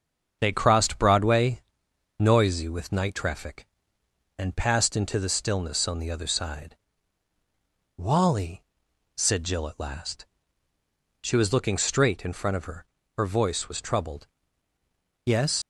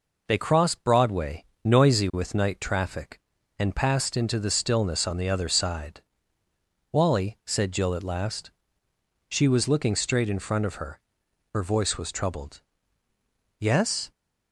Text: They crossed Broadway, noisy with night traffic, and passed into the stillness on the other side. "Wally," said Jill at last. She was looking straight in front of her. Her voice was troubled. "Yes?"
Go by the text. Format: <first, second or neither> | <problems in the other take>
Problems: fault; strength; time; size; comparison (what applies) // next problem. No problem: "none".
second | starts louder than the rest; until 1.4 s; 7 dB // leaves "Yes" unfinished; at 15.6 s; 115 ms